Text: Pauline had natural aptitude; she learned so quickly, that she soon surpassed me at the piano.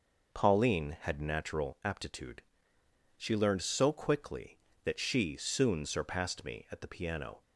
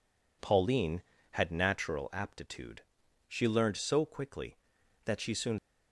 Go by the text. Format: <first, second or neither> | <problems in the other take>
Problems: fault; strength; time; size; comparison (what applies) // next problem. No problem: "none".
first | stops before "surpassed me at the piano"; at 5.5 s